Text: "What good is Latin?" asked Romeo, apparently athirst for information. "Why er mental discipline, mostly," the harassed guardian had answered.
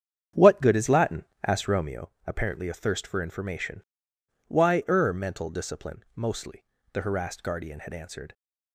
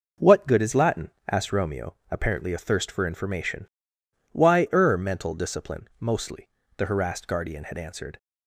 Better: second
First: starts louder than the rest; strong; until 2.0 s; 8.5 dB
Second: none

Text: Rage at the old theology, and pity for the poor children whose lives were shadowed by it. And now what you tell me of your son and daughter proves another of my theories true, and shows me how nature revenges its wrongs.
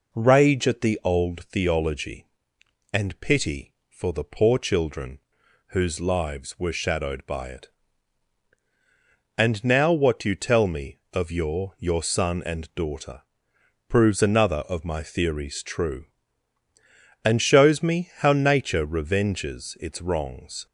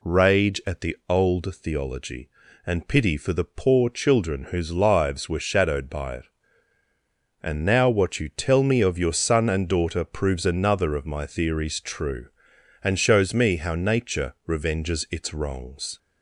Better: second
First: pauses between "children" and "whose"; noticeable; at 5.1 s; 0.48 s long // says "your" twice; at 11.7 s // pauses between "daughter" and "proves"; noticeable; at 13.2 s; 0.66 s long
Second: none

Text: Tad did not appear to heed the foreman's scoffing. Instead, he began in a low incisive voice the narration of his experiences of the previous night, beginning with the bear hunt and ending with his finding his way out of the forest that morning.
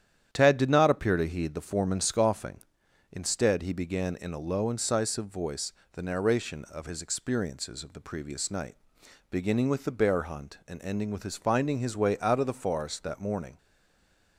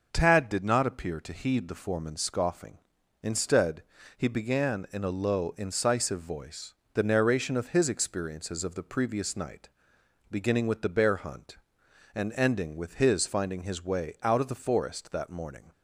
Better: second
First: starts louder than the rest; strong; until 1.3 s; 10 dB // pauses between "voice" and "the"; slight; at 5.7 s; 0.20 s long // stays silent after the last word; slight; from 13.5 s on; 0.8 s long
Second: pauses between "voice" and "the"; slight; at 6.7 s; 0.20 s long

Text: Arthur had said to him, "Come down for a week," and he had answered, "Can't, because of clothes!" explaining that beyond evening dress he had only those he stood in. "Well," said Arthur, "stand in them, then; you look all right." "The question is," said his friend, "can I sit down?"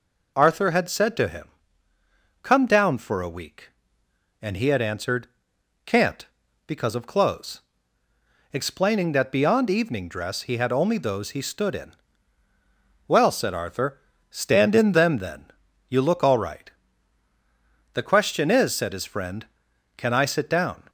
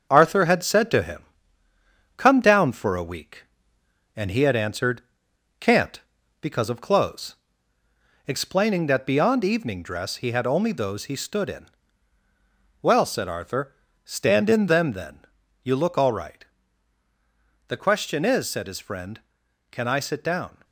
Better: first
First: none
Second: gets quieter; noticeable; throughout; 6 dB

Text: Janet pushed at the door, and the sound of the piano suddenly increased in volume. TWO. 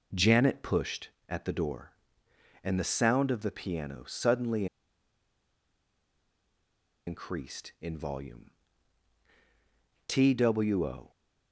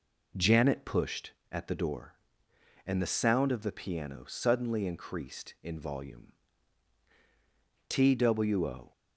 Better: second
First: pauses between "suddenly" and "increased"; strong; at 4.6 s; 2.4 s long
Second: none

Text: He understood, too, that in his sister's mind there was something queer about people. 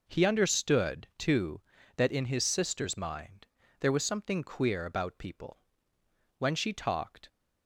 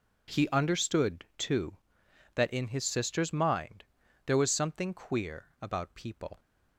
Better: second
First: pauses between "mind" and "there"; slight; at 3.4 s; 0.34 s long // goes on to say "When she talked"; noticeable; from 6.3 s on; 0.90 s long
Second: pauses between "mind" and "there"; at 3.8 s; 0.44 s long

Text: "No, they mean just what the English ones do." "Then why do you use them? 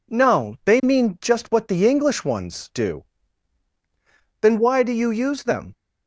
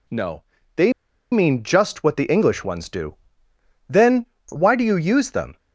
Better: first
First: none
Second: pauses between "they" and "mean"; at 0.9 s; 0.40 s long // pauses between "Then" and "why"; slight; at 4.2 s; 0.22 s long

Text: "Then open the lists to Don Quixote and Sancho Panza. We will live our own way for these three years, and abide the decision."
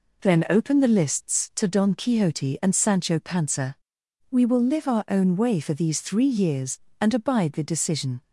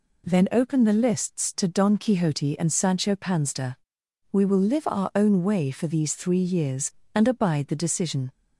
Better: neither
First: none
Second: none

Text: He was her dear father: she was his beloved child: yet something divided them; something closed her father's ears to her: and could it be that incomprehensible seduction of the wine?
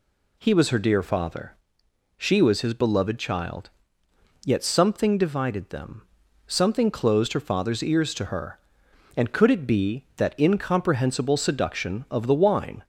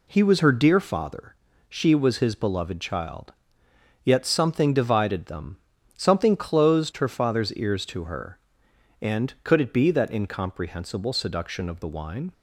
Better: neither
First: none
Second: none

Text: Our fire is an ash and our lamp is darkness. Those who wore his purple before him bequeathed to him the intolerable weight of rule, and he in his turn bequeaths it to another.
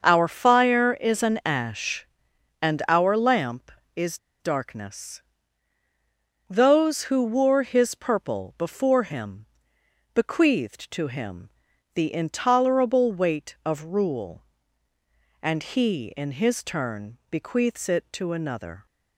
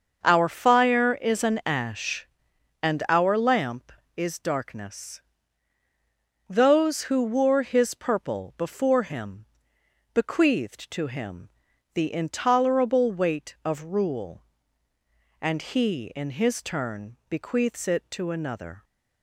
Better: second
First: starts louder than the rest; until 1.0 s; 6.5 dB // pauses between "is" and "darkness"; slight; at 4.1 s; 0.24 s long // pauses between "him" and "bequeathed"; noticeable; at 9.4 s; 0.68 s long // pauses between "him" and "the"; noticeable; at 11.4 s; 0.46 s long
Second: starts louder than the rest; until 1.2 s; 6.5 dB // pauses between "him" and "bequeathed"; noticeable; at 9.4 s; 0.68 s long // pauses between "him" and "the"; noticeable; at 11.4 s; 0.46 s long

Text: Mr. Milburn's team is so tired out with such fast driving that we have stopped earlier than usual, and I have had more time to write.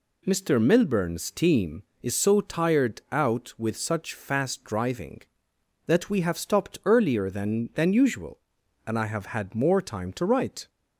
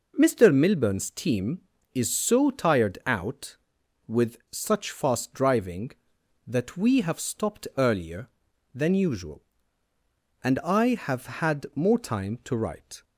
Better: second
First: says "than" twice; at 7.7 s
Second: none

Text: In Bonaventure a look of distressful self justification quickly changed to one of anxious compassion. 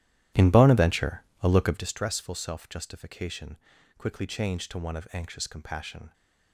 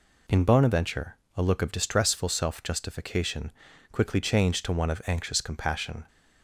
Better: second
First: starts louder than the rest; strong; until 1.9 s; 13 dB // pauses between "Bonaventure" and "a"; slight; at 1.2 s; 0.18 s long // pauses between "justification" and "quickly"; at 3.5 s; 0.40 s long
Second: pauses between "Bonaventure" and "a"; slight; at 1.1 s; 0.18 s long // pauses between "justification" and "quickly"; at 3.5 s; 0.40 s long

